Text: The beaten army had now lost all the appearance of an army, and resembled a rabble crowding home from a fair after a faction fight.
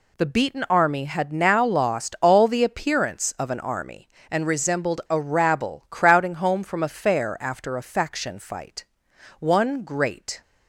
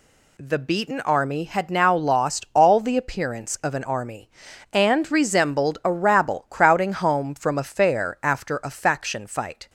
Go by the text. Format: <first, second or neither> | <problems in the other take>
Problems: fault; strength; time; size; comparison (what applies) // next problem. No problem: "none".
second | goes on to say "One great"; noticeable; from 9.3 s on; 1.0 s long